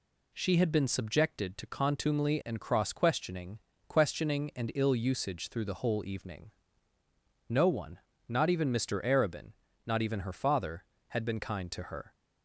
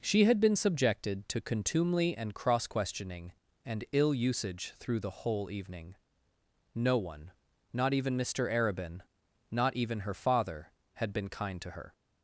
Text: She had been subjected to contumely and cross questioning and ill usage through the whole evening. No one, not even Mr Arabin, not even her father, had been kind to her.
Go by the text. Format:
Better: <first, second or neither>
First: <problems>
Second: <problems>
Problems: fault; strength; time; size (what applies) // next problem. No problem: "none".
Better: second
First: says "questioning" twice; at 3.8 s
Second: none